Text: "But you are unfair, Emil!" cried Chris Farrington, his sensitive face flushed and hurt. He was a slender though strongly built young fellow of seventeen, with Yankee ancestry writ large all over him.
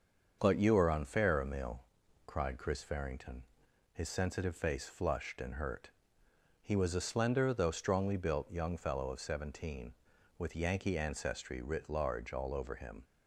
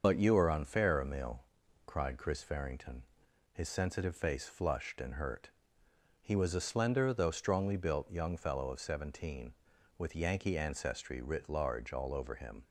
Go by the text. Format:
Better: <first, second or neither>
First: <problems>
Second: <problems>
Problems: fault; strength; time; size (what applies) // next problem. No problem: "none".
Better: first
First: starts louder than the rest; until 1.4 s; 6.5 dB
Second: loses the start of "But"; at 0.0 s; 40 ms // starts louder than the rest; until 1.0 s; 6.5 dB